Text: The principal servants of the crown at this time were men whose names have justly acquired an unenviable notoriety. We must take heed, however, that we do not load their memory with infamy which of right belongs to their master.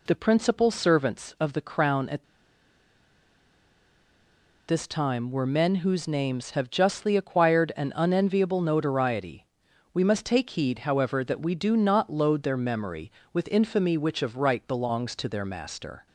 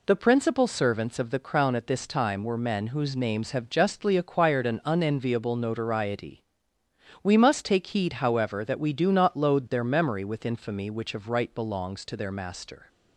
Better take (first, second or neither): second